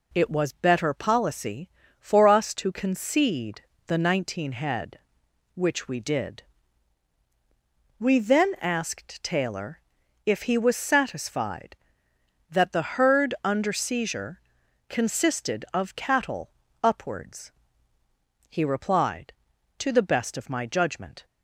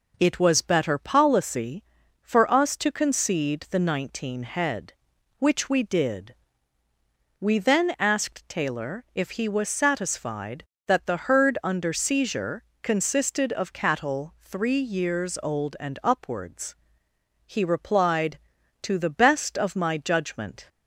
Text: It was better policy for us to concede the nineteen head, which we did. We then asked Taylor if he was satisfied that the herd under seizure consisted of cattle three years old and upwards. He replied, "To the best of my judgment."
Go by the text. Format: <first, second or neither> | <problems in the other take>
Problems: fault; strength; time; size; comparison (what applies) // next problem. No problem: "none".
second | pauses between "concede" and "the"; slight; at 3.6 s; 0.26 s long // pauses between "Taylor" and "if"; noticeable; at 9.8 s; 0.46 s long // pauses between "seizure" and "consisted"; noticeable; at 14.4 s; 0.48 s long; slight in the second // skips "three years old and"; at 16.6 s